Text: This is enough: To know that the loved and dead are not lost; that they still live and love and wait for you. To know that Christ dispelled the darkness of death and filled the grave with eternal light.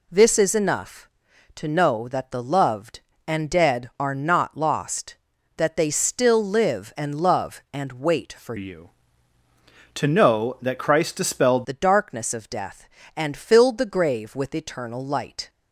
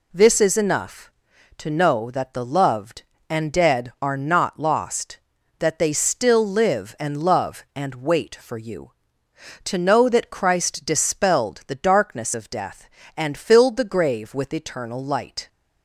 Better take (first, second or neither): second